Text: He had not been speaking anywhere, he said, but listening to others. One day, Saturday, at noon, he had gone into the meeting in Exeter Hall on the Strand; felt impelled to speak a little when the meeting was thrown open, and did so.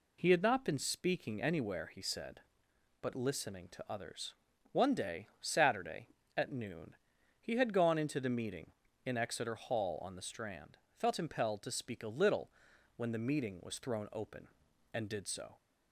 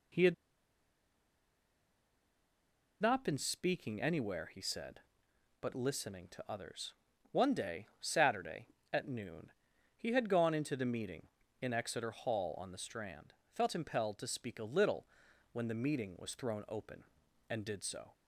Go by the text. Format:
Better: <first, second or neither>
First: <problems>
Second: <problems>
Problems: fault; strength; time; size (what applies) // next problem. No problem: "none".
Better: first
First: pauses between "little" and "when"; at 12.5 s; 0.44 s long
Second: pauses between "had" and "not"; strong; at 0.3 s; 2.6 s long // pauses between "little" and "when"; at 15.0 s; 0.44 s long